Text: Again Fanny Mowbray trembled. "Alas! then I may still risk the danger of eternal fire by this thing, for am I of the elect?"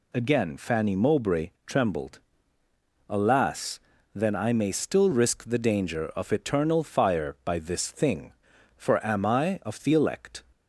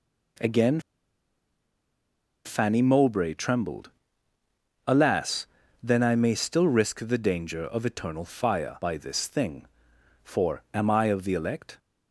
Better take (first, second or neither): first